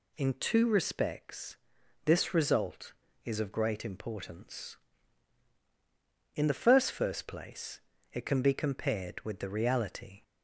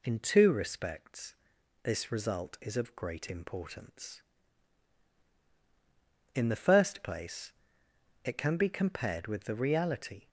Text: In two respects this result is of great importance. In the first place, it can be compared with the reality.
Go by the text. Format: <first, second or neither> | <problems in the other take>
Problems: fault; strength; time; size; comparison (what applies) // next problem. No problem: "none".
second | pauses between "respects" and "this"; noticeable; at 1.5 s; 0.50 s long; noticeable in the second // says "first" twice; at 6.9 s